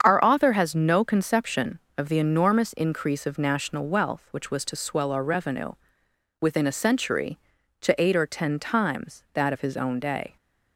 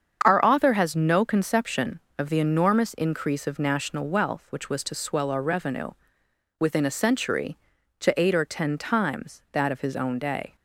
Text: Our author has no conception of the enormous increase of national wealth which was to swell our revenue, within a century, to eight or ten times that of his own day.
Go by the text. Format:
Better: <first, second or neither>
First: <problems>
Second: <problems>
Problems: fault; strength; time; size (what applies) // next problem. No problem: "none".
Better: neither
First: starts louder than the rest; strong; until 1.0 s; 7.5 dB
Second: starts louder than the rest; strong; until 1.2 s; 7.5 dB